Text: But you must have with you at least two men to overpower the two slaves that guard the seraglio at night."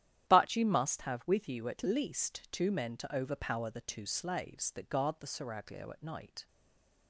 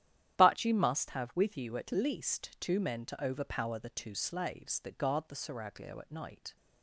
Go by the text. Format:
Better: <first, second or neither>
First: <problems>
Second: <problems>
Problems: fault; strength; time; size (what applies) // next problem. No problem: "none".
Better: second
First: starts louder than the rest; strong; until 1.3 s; 11.5 dB // stays silent after the last word; slight; from 6.4 s on; 0.6 s long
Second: starts louder than the rest; strong; until 1.4 s; 11.5 dB